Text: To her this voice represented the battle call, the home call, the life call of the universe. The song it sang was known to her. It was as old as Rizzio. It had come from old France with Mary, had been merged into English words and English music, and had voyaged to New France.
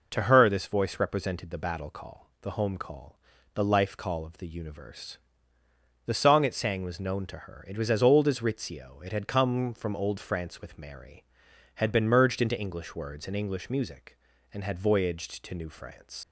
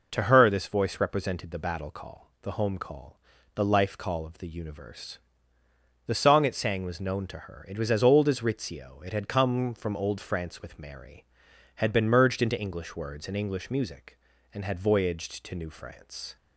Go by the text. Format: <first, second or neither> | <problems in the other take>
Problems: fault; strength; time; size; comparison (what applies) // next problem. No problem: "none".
second | leaves "France" unfinished; at 16.2 s; 125 ms